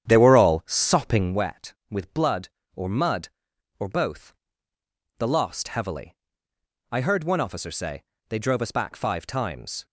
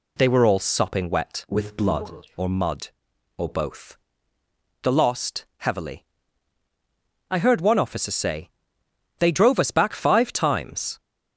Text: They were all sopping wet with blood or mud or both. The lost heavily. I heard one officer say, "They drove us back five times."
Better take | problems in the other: second | starts louder than the rest; strong; until 1.4 s; 9.5 dB

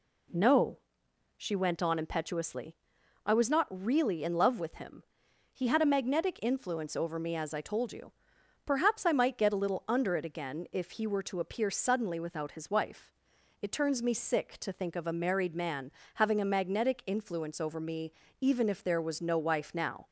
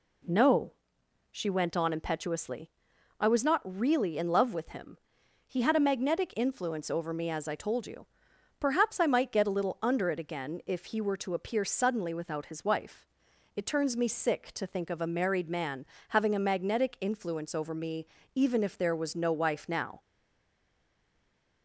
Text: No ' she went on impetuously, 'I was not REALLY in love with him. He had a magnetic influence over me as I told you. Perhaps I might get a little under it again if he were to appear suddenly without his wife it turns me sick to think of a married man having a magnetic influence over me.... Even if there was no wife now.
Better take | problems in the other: first | pauses between "wife" and "it"; noticeable; at 13.0 s; 0.46 s long; noticeable in the first // pauses between "man" and "having"; slight; at 15.8 s; 0.24 s long; slight in the first // stays silent after the last word; noticeable; from 20.0 s on; 1.6 s long

